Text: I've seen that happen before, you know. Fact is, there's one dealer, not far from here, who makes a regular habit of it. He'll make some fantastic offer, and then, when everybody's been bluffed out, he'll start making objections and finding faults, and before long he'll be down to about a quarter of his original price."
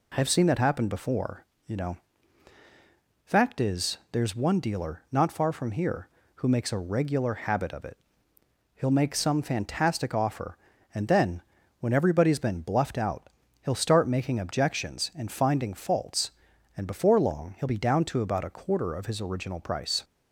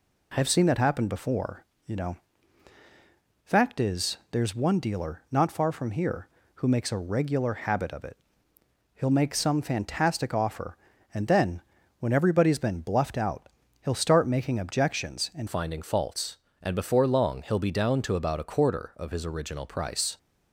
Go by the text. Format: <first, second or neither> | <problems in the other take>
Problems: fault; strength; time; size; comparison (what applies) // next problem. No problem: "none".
first | changes voice at "finding"; from 15.4 s on; 4.7 s long